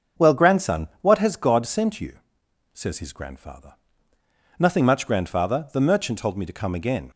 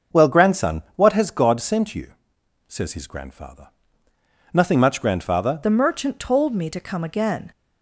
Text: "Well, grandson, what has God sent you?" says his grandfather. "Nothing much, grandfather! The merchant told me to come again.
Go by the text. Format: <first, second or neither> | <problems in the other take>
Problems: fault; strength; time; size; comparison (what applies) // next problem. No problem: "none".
first | starts louder than the rest; until 1.2 s; 6.5 dB; also in the first // changes voice at "The"; from 5.6 s on; 1.9 s long